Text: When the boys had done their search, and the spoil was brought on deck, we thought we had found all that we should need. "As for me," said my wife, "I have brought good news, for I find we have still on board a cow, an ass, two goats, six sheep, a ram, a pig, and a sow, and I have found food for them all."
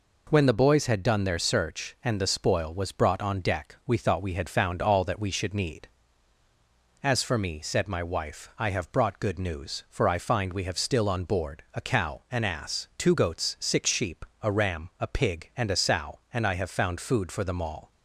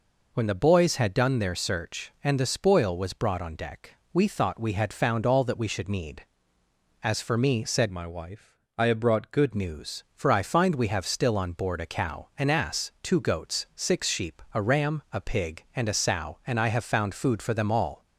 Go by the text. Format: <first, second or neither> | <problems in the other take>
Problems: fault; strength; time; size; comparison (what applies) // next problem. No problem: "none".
first | changes voice from "my" to "good"; from 7.9 to 9.5 s; 1.6 s long